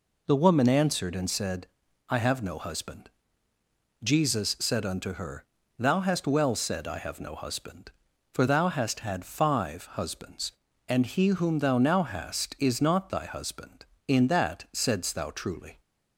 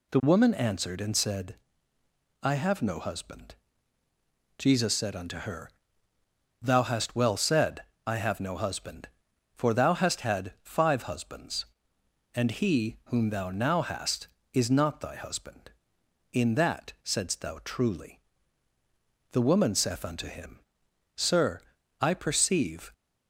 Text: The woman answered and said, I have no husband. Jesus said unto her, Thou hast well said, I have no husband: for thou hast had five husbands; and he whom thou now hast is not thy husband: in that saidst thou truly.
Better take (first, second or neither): first